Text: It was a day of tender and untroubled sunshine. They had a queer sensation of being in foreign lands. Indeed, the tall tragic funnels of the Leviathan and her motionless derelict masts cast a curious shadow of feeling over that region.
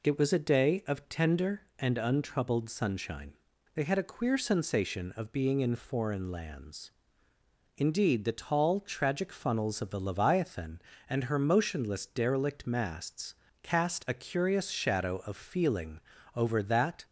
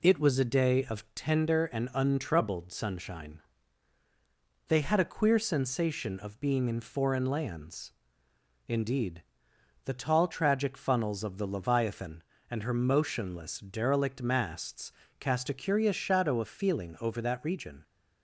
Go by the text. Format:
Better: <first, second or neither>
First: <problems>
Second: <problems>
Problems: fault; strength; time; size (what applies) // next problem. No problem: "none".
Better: second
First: pauses between "masts" and "cast"; slight; at 13.3 s; 0.28 s long // pauses between "feeling" and "over"; slight; at 15.9 s; 0.34 s long // stops before "region"; at 17.0 s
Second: pauses between "masts" and "cast"; slight; at 14.9 s; 0.26 s long